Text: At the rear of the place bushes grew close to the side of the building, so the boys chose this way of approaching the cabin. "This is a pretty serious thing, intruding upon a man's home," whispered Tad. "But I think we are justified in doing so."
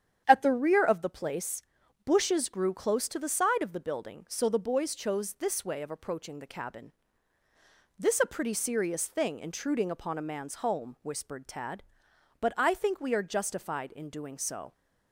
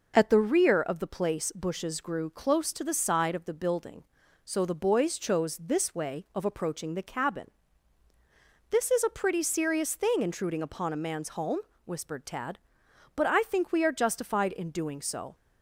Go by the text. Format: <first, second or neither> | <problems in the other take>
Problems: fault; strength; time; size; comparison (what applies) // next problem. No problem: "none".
second | starts louder than the rest; strong; until 1.2 s; 9 dB // pauses between "place" and "bushes"; at 1.6 s; 0.44 s long // skips "is"; at 8.1 s